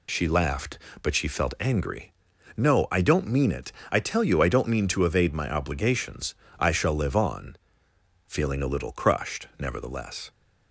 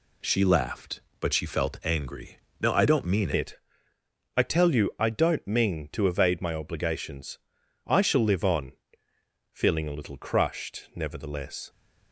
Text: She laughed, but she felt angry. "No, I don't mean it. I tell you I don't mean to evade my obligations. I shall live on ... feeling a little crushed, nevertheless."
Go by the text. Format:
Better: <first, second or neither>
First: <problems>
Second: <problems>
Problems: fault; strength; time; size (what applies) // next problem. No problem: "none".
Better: first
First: none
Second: changes voice at "it"; from 3.3 s on; 8.3 s long